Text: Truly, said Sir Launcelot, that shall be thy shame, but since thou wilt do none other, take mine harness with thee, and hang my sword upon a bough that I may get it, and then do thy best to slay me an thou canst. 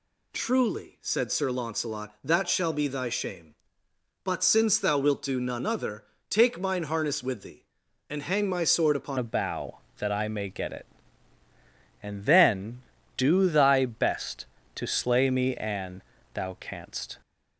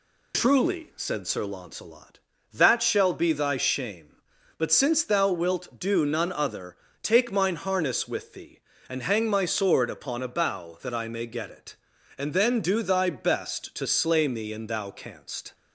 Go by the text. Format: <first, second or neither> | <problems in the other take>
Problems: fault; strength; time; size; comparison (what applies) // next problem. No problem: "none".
second | changes voice at "a"; from 9.1 s on; 8.0 s long // pauses between "an" and "thou"; slight; at 16.0 s; 0.32 s long